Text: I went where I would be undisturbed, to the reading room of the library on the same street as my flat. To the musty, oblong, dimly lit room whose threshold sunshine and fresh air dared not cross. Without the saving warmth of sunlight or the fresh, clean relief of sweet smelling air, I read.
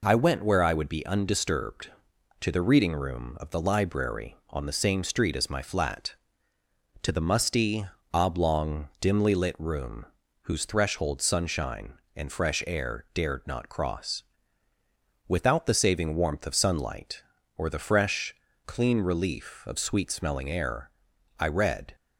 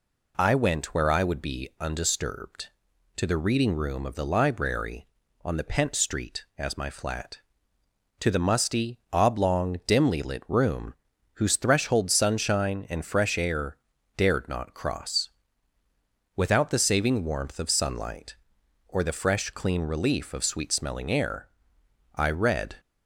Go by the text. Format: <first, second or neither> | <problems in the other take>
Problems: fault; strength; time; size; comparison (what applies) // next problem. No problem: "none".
first | says "pent" for "same"; at 5.6 s // pauses between "room" and "whose"; at 10.9 s; 0.40 s long; also in the first // pauses between "air" and "dared"; at 13.7 s; 0.40 s long